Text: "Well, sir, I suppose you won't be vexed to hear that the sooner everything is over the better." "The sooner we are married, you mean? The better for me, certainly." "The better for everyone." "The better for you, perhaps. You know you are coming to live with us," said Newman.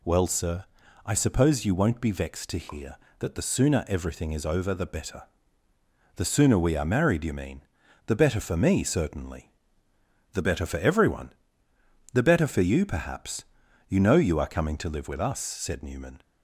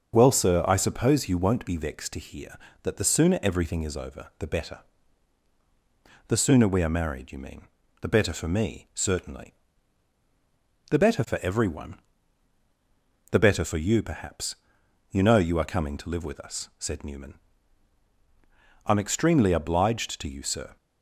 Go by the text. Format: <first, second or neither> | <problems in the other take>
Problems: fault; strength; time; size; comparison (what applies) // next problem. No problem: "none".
first | starts louder than the rest; until 1.1 s; 6.5 dB // goes on to say "I'm extremely obliged to you sir"; strong; from 18.8 s on; 1.9 s long